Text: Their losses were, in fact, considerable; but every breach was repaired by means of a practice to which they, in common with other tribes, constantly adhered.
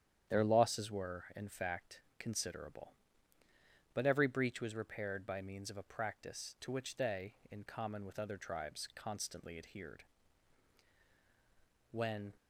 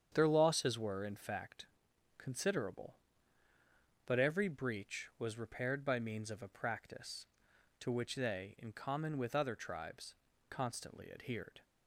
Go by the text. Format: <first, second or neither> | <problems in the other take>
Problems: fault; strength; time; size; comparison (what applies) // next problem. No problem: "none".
second | starts louder than the rest; strong; until 1.4 s; 9.5 dB; strong in the second // goes on to say "When"; slight; from 11.9 s on; 0.42 s long